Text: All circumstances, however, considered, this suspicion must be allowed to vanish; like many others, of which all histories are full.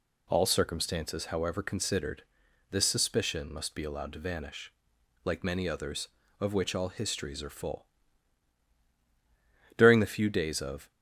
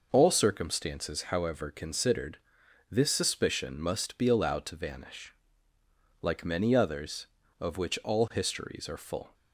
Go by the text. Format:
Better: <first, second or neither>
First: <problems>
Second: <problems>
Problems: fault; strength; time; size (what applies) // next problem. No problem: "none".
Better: second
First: goes on to say "During the few days of"; noticeable; from 9.7 s on; 1.1 s long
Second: none